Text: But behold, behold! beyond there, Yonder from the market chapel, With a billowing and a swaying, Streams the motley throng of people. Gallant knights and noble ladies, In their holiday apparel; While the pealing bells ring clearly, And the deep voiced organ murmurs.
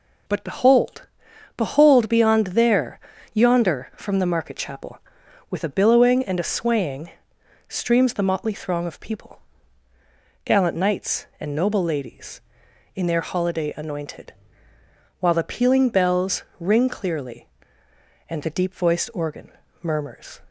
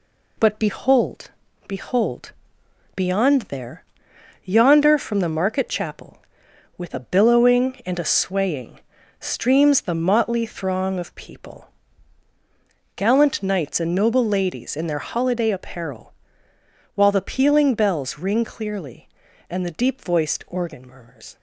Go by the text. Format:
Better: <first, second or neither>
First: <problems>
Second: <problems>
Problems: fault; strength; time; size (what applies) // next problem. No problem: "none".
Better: second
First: says "anointed" for "apparel"; at 13.7 s // pauses between "bells" and "ring"; slight; at 16.4 s; 0.16 s long // pauses between "organ" and "murmurs"; slight; at 19.5 s; 0.28 s long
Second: none